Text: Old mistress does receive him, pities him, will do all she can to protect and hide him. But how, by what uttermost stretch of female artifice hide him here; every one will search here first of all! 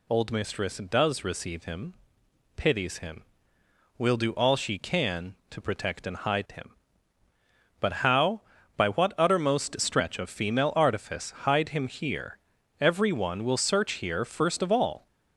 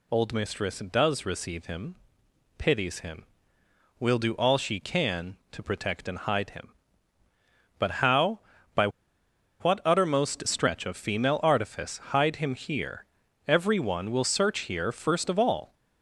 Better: first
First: none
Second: pauses between "by" and "what"; noticeable; at 8.8 s; 0.73 s long

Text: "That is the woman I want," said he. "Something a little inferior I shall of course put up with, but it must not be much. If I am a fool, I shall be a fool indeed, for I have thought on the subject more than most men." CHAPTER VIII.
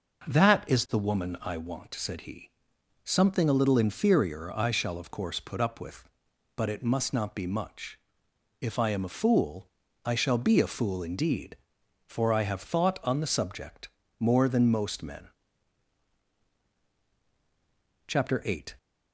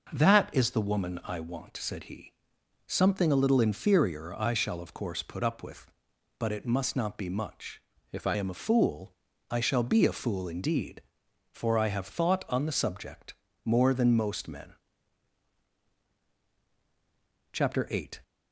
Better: first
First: pauses between "subject" and "more"; slight; at 13.8 s; 0.30 s long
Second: changes voice from "If" to "I"; from 8.1 to 8.3 s; 0.2 s long // pauses between "subject" and "more"; slight; at 13.3 s; 0.30 s long

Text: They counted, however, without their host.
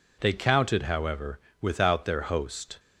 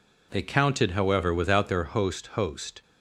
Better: first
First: none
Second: says "host" twice; at 2.2 s

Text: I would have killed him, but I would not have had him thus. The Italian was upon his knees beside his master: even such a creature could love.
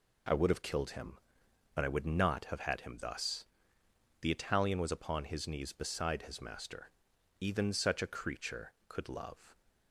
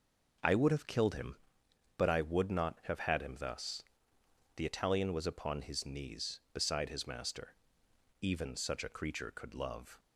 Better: first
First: none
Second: starts louder than the rest; noticeable; until 1.6 s; 5.5 dB

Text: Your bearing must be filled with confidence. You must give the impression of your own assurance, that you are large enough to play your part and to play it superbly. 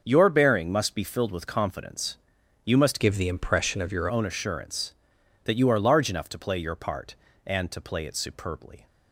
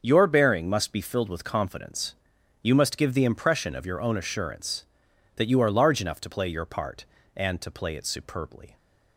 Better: second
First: starts louder than the rest; until 1.0 s; 6.5 dB // changes voice from "give" to "your"; from 3.0 to 4.0 s; 1.0 s long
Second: starts louder than the rest; until 1.0 s; 7 dB

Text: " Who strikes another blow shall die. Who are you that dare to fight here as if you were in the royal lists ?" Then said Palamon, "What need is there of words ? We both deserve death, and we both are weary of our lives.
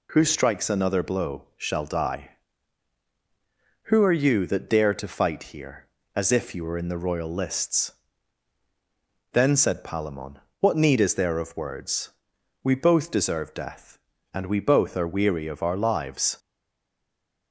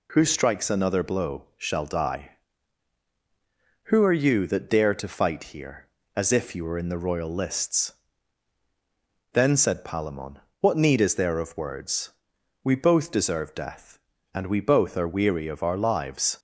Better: second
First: stays silent after the last word; from 16.3 s on; 1.2 s long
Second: none

